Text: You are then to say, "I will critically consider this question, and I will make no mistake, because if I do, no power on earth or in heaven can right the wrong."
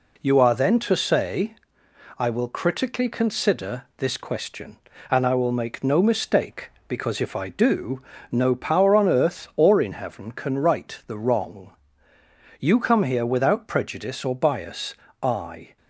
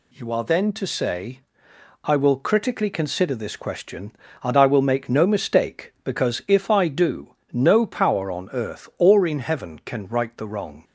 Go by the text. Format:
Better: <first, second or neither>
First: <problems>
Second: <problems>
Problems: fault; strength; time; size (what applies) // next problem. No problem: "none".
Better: second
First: goes on to say "You come here without prejudice or bias I"; strong; from 12.5 s on; 3.1 s long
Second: none